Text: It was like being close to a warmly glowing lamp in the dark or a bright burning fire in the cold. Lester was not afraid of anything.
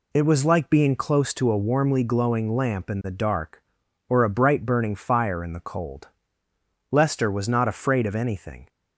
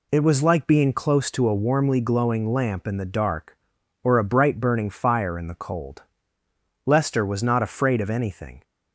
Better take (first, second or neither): neither